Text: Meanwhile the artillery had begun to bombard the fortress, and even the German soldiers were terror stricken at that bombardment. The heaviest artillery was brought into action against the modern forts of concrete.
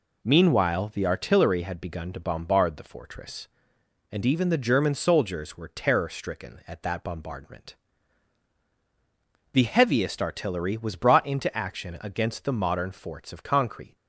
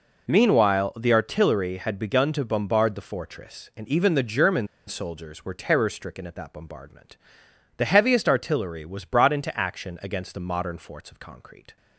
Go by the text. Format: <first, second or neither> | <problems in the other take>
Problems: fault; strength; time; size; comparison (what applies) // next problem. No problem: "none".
first | pauses between "German" and "soldiers"; slight; at 4.6 s; 0.20 s long